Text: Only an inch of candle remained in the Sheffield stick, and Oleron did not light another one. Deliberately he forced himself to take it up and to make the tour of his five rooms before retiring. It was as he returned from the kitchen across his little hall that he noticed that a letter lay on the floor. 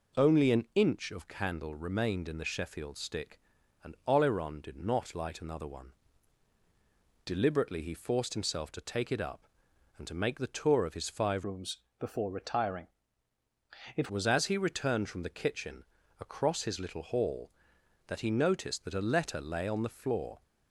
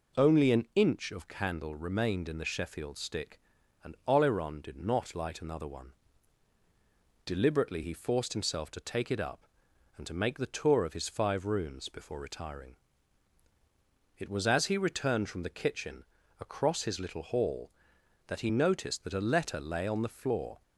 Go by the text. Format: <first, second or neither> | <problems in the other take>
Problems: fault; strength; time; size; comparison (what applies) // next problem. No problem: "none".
second | changes voice from "rooms" to "It"; from 11.4 to 14.0 s; 2.6 s long // pauses between "rooms" and "before"; slight; at 11.7 s; 0.22 s long // pauses between "kitchen" and "across"; slight; at 15.8 s; 0.36 s long; slight in the second